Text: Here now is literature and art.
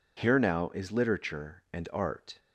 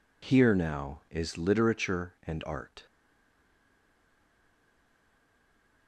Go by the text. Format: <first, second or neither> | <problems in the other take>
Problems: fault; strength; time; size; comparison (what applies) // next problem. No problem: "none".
first | stays silent after the last word; strong; from 2.8 s on; 3.0 s long